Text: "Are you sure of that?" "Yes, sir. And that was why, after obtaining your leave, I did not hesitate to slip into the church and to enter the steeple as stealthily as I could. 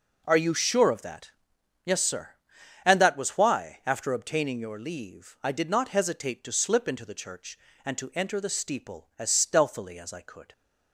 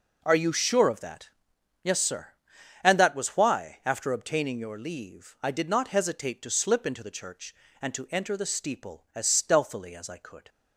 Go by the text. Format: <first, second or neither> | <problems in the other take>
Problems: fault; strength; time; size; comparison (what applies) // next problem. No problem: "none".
neither | none